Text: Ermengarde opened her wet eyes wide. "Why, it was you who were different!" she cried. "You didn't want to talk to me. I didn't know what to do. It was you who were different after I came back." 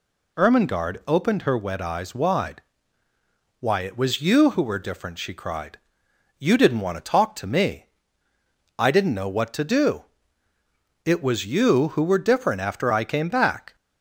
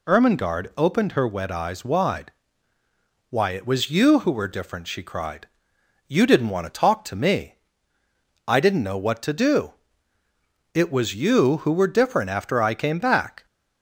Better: neither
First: none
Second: none

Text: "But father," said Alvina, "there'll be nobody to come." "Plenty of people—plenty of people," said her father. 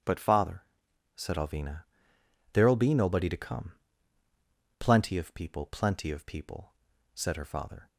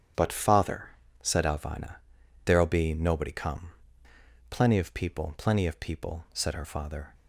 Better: first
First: starts louder than the rest; strong; until 1.5 s; 9 dB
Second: starts louder than the rest; strong; until 1.4 s; 9 dB // skips "to"; at 3.3 s

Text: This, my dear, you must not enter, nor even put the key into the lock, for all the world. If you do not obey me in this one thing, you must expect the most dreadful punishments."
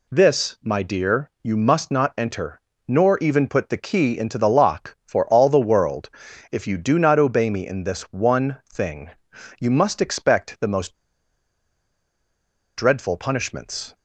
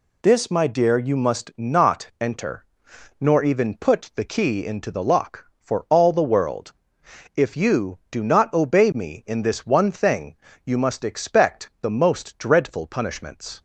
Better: second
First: pauses between "one" and "thing"; slight; at 8.5 s; 0.16 s long // pauses between "most" and "dreadful"; strong; at 10.9 s; 1.8 s long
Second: none

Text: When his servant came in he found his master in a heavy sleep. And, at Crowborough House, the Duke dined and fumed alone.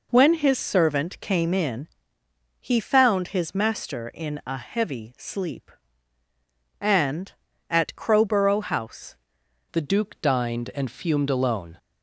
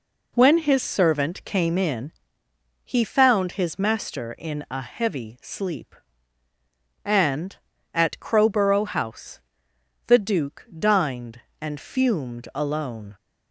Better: second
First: pauses between "in" and "he"; noticeable; at 1.8 s; 0.74 s long // changes voice at "the"; from 9.7 s on; 2.0 s long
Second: pauses between "in" and "he"; noticeable; at 2.1 s; 0.74 s long

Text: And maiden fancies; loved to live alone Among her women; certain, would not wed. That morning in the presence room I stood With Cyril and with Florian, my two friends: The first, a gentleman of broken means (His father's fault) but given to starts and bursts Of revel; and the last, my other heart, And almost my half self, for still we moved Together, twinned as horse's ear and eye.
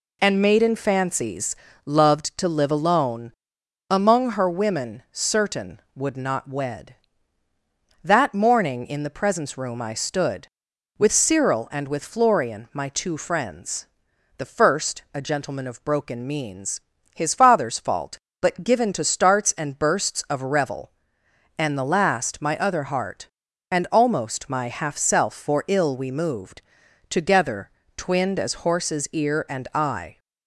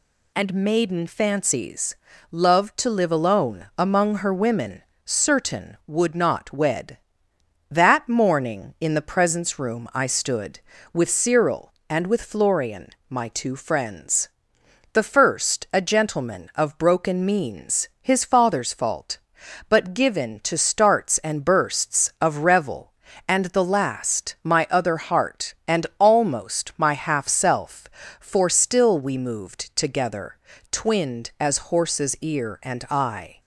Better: second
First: pauses between "alone" and "Among"; noticeable; at 3.3 s; 0.56 s long // says "ill" for "still"; at 25.6 s // pauses between "moved" and "Together"; noticeable; at 26.6 s; 0.48 s long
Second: none

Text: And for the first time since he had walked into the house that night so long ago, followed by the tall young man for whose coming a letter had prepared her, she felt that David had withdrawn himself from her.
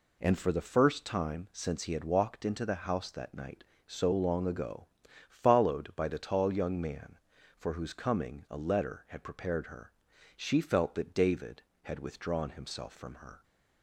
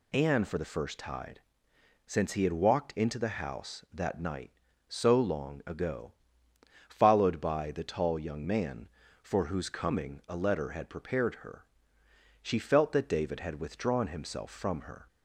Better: first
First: none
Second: says "tide" for "time"; at 0.9 s

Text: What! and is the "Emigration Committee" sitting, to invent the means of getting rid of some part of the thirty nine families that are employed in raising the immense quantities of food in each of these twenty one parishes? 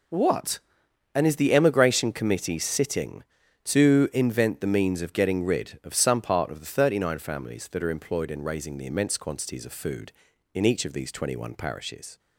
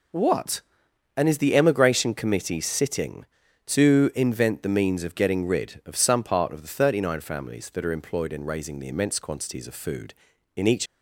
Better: first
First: none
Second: stops before "of these twenty one parishes"; at 10.8 s

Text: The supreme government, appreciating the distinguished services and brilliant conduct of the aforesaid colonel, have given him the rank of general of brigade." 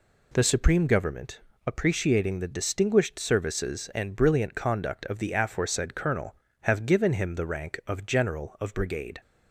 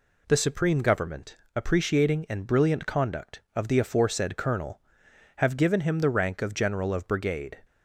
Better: first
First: none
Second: skips "the distinguished services"; at 2.2 s

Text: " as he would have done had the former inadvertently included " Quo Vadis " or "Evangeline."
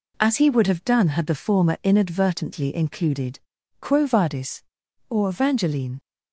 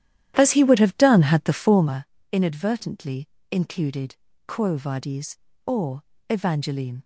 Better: first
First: none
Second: starts louder than the rest; strong; until 1.9 s; 12 dB // pauses between "former" and "inadvertently"; slight; at 2.0 s; 0.30 s long // pauses between "inadvertently" and "included"; slight; at 3.2 s; 0.22 s long // pauses between "or" and "Evangeline"; slight; at 6.0 s; 0.26 s long

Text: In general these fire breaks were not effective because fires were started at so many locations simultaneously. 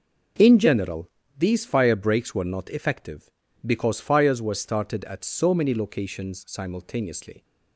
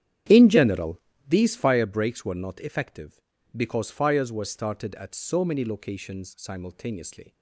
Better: first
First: pauses between "general" and "these"; slight; at 1.0 s; 0.30 s long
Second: starts louder than the rest; strong; until 1.8 s; 10 dB // pauses between "general" and "these"; slight; at 0.9 s; 0.30 s long

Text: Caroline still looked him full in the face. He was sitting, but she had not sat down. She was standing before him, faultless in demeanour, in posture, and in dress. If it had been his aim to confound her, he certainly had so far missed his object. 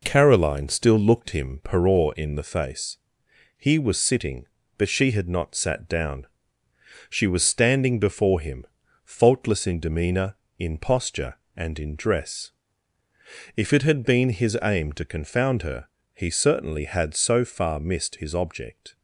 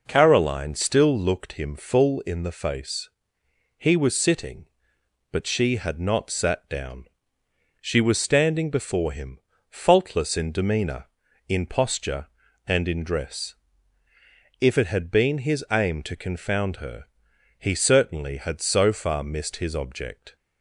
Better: second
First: says "peror" for "full"; at 1.6 s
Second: none

